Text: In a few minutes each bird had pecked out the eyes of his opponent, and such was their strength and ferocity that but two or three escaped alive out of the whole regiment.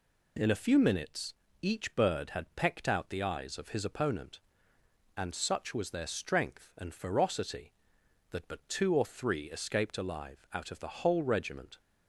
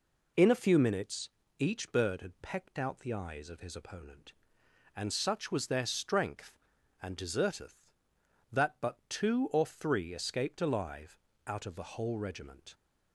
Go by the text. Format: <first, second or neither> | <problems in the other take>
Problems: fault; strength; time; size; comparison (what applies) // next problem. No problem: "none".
first | pauses between "minutes" and "each"; slight; at 1.2 s; 0.30 s long; slight in the first // says "deserteth" for "ferocity"; at 7.1 s // pauses between "alive" and "out"; slight; at 11.1 s; 0.26 s long